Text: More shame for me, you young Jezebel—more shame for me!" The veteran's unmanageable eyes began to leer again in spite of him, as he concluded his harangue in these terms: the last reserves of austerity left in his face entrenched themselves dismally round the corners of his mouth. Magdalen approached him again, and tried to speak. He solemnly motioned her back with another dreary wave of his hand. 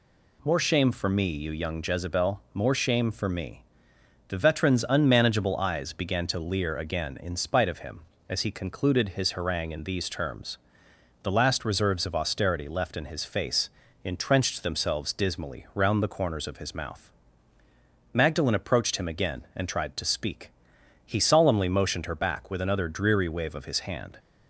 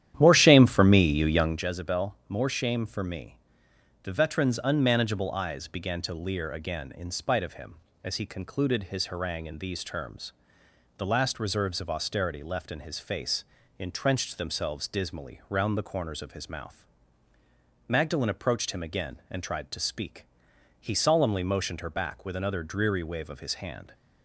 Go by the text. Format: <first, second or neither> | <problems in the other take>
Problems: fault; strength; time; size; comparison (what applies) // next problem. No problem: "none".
first | starts louder than the rest; strong; until 1.7 s; 11 dB // pauses between "face" and "entrenched"; slight; at 13.4 s; 0.34 s long; slight in the first